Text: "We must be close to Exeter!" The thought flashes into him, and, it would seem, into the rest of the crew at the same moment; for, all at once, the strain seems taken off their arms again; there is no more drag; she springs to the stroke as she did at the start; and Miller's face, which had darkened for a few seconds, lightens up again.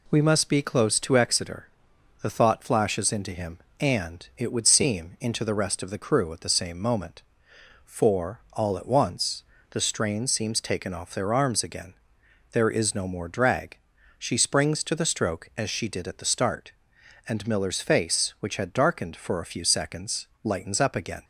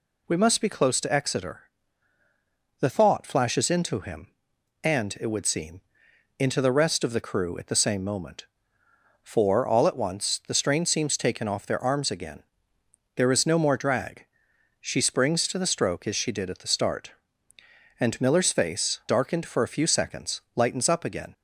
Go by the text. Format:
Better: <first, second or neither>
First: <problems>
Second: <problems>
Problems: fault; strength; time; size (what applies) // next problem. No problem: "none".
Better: first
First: none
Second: skips "which had"; at 19.0 s